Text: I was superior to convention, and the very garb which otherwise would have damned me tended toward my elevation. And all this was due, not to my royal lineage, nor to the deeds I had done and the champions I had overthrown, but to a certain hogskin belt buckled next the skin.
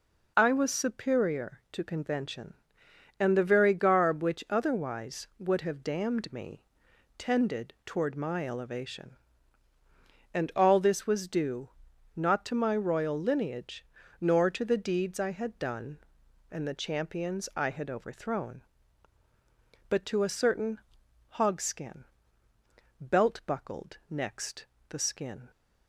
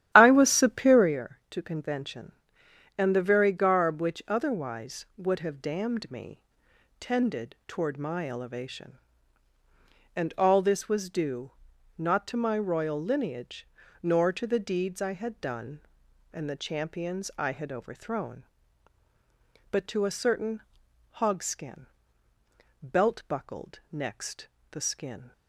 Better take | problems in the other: first | starts louder than the rest; strong; until 1.2 s; 12.5 dB // pauses between "me" and "tended"; noticeable; at 6.4 s; 0.58 s long; noticeable in the first // pauses between "certain" and "hogskin"; noticeable; at 20.6 s; 0.58 s long; noticeable in the first // pauses between "hogskin" and "belt"; noticeable; at 21.8 s; 0.96 s long; noticeable in the first // pauses between "next" and "the"; slight; at 24.4 s; 0.24 s long; slight in the first

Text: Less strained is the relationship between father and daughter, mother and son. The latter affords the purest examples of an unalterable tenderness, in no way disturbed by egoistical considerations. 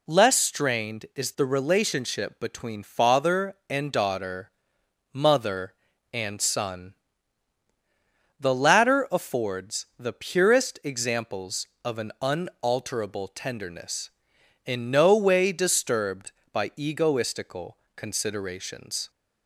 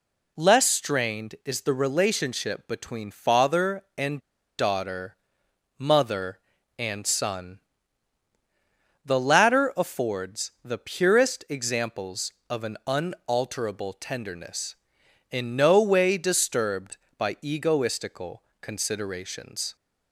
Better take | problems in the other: first | pauses between "and" and "daughter"; at 4.1 s; 0.40 s long // pauses between "egoistical" and "considerations"; slight; at 18.4 s; 0.18 s long; slight in the first

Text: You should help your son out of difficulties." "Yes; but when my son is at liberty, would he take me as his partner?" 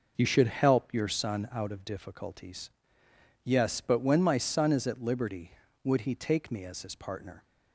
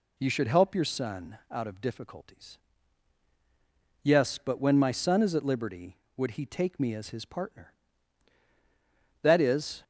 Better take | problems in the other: first | goes on to say "That is"; noticeable; from 9.2 s on; 0.62 s long

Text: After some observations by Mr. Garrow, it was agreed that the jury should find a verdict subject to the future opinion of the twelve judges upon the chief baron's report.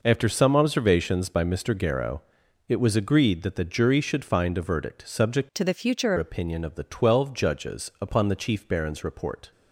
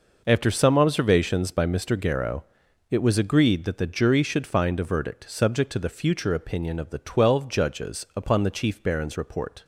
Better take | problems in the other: second | changes voice from "to" to "future"; from 5.5 to 6.1 s; 0.6 s long

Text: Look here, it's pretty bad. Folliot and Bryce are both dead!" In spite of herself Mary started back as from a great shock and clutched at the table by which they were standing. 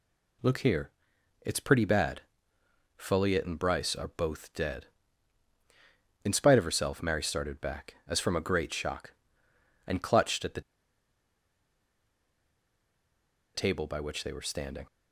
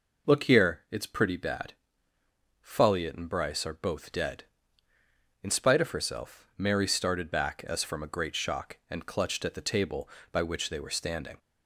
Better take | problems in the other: second | pauses between "the" and "table"; strong; at 10.6 s; 2.9 s long

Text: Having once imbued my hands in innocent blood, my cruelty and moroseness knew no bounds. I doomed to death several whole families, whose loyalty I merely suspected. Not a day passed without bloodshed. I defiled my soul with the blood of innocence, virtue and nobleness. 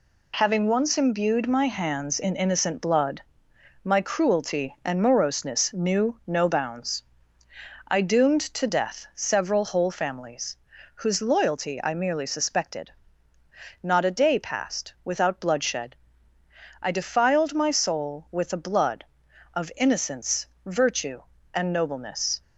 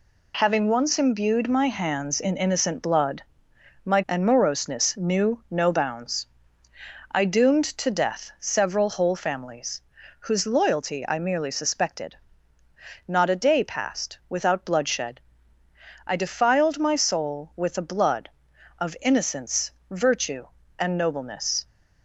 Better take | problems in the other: first | skips "cruelty"; at 4.0 s

